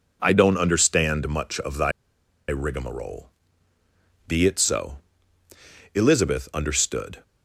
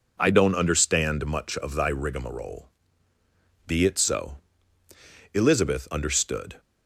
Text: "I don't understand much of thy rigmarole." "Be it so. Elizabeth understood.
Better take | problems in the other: second | pauses between "thy" and "rigmarole"; noticeable; at 1.9 s; 0.57 s long

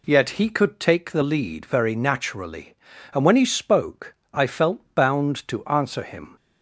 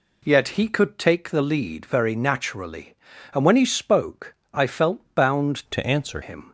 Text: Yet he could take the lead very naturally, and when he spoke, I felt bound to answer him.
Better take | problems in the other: first | changes voice from "to" to "answer"; from 5.7 to 6.2 s; 0.5 s long

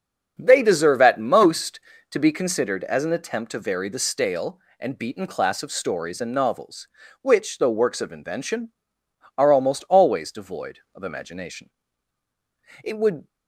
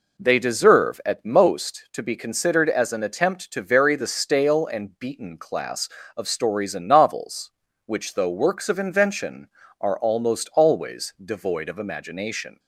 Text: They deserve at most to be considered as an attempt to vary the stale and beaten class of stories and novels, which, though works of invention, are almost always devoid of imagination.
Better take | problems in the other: second | starts louder than the rest; until 1.3 s; 7 dB // goes on to say "It would"; slight; from 12.8 s on; 0.44 s long

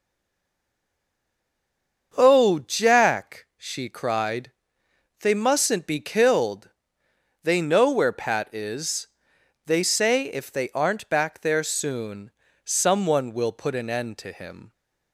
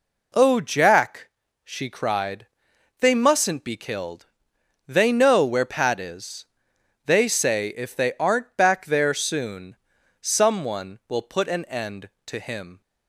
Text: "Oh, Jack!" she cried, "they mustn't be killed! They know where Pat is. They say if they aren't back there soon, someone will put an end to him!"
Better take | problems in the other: second | stays silent before the first word; until 2.1 s; 2.1 s long // starts louder than the rest; until 3.1 s; 6.5 dB

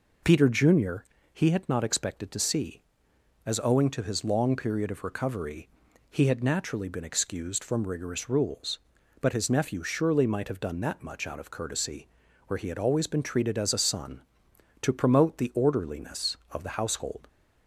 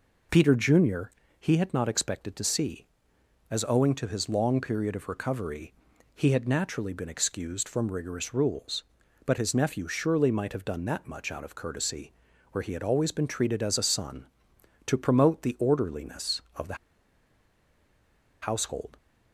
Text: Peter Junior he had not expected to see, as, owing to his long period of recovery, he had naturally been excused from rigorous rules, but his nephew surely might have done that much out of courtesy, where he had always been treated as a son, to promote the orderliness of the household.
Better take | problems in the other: first | pauses between "Junior" and "he"; slight; at 1.1 s; 0.30 s long; slight in the first // pauses between "the" and "household"; strong; at 16.7 s; 1.6 s long

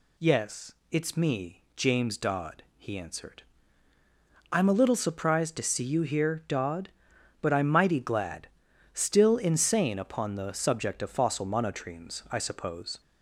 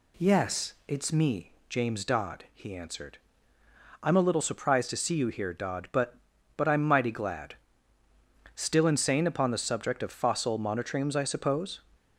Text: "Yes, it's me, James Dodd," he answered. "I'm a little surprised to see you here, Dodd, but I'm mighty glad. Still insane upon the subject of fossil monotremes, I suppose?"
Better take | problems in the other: first | says "but" twice; at 6.5 s

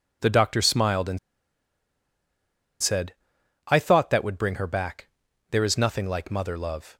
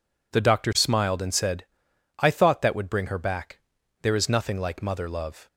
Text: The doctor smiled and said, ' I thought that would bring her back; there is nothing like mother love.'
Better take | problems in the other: second | pauses between "and" and "said"; strong; at 1.1 s; 1.6 s long

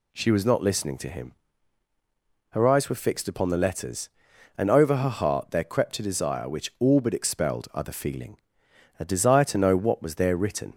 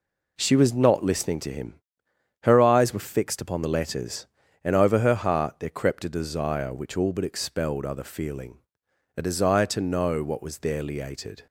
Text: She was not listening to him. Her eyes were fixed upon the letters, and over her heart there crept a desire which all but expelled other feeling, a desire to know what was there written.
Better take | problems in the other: first | says "liated" for "written"; at 10.8 s

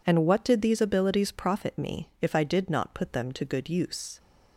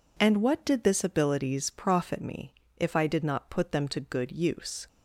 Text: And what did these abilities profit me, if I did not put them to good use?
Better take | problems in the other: first | says "this" for "these"; at 0.8 s

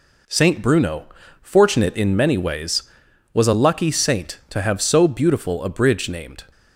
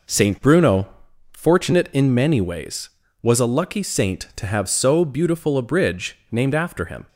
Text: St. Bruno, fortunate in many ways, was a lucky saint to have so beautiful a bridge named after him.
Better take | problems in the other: second | stops before "after him"; at 6.5 s

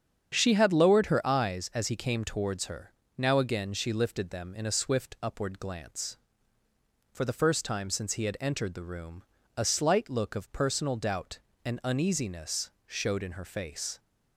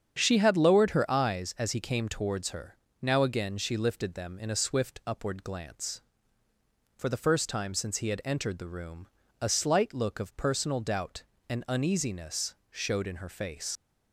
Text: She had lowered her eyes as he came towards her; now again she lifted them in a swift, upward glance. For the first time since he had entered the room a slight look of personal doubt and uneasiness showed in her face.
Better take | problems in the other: first | starts louder than the rest; strong; until 1.1 s; 8 dB; strong in the first // pauses between "room" and "a"; slight; at 9.0 s; 0.30 s long; slight in the first // pauses between "uneasiness" and "showed"; slight; at 12.5 s; 0.16 s long; slight in the first // leaves "face" unfinished; at 13.7 s; 80 ms

